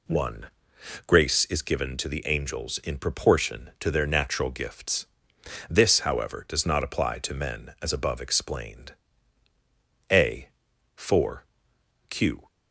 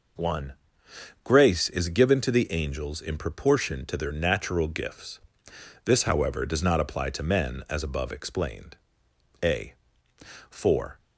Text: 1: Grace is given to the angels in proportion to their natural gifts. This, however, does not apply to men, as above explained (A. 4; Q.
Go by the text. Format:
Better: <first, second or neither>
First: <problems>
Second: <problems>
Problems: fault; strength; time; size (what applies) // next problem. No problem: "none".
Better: first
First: none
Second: stops before "Q"; at 10.9 s